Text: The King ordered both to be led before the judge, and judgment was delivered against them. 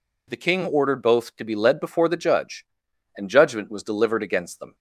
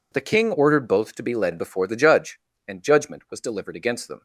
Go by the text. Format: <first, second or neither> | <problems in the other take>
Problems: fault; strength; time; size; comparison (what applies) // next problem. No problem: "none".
neither | none